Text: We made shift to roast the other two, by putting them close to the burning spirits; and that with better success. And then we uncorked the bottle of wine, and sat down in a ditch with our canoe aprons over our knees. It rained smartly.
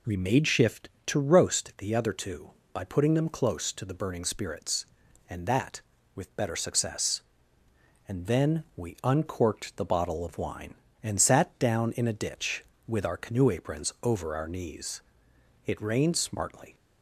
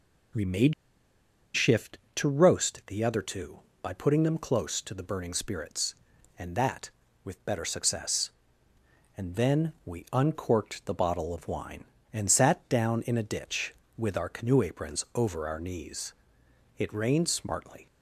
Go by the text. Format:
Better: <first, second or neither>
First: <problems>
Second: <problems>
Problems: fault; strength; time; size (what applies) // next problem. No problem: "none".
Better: first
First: none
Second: pauses between "made" and "shift"; noticeable; at 0.7 s; 0.80 s long